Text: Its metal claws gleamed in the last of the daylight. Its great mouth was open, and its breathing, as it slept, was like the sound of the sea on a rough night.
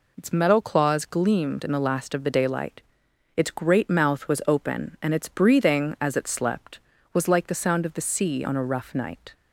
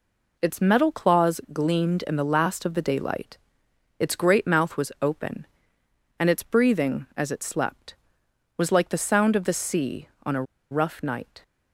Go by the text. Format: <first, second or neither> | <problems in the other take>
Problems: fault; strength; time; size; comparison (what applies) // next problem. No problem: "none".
first | pauses between "a" and "rough"; slight; at 10.4 s; 0.27 s long